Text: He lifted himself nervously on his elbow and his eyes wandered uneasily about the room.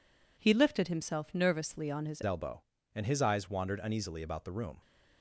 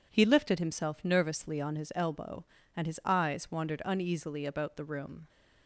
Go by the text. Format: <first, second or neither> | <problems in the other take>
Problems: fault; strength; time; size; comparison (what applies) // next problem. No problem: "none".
second | changes voice at "elbow"; from 2.2 s on; 2.6 s long